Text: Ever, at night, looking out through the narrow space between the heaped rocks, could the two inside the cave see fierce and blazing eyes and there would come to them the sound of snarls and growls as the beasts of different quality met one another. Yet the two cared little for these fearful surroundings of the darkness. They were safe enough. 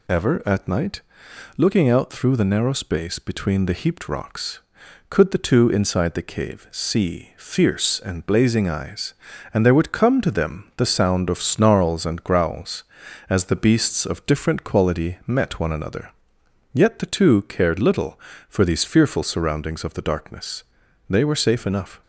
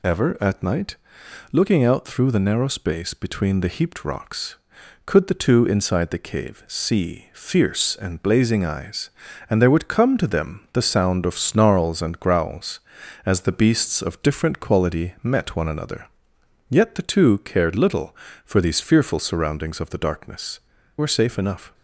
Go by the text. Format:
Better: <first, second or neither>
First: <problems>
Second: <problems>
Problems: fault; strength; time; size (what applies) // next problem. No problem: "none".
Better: first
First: none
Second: skips "They"; at 20.7 s